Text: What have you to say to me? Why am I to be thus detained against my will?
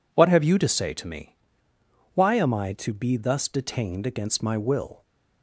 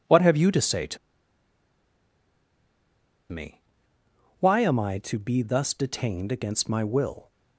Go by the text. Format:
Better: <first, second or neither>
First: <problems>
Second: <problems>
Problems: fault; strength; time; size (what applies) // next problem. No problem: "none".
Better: first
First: none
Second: pauses between "to" and "me"; strong; at 0.9 s; 2.3 s long